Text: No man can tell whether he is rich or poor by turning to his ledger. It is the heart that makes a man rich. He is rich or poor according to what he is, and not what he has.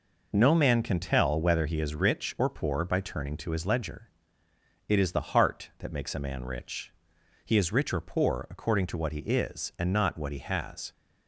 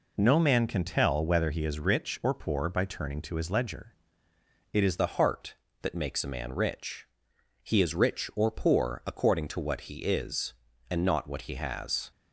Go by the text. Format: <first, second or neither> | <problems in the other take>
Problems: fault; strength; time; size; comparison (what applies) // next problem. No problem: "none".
first | changes voice at "the"; from 4.9 s on; 7.2 s long